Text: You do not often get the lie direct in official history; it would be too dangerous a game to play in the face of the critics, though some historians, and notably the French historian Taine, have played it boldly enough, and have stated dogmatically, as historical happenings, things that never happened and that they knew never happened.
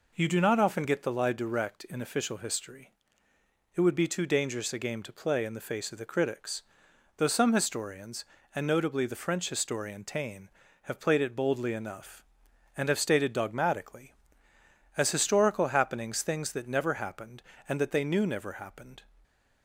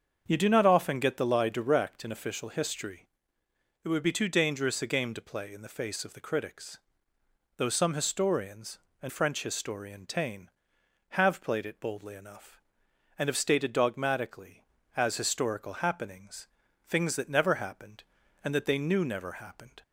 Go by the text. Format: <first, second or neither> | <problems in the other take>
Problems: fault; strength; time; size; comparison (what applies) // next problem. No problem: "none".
first | starts louder than the rest; until 1.2 s; 7 dB // skips "notably the"; at 9.0 s